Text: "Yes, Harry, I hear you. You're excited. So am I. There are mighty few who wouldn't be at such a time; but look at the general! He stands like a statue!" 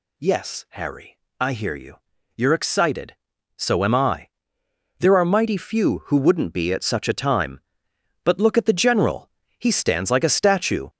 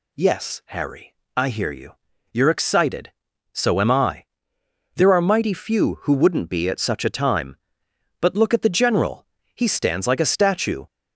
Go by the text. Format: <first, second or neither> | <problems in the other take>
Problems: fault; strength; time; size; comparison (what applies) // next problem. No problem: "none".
second | gets louder; noticeable; throughout; 6 dB